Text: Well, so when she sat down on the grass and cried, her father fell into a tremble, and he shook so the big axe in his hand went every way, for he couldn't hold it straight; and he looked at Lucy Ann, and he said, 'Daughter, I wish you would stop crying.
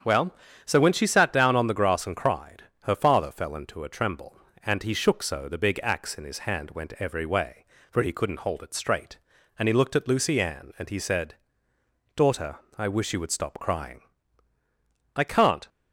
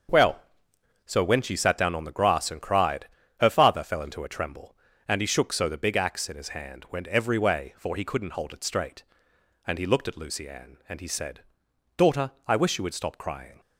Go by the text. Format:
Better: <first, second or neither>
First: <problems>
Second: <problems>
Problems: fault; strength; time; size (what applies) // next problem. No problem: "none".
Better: second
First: starts louder than the rest; strong; until 1.3 s; 7.5 dB // goes on to say "I can't"; from 15.1 s on; 0.52 s long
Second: starts louder than the rest; until 1.7 s; 6.5 dB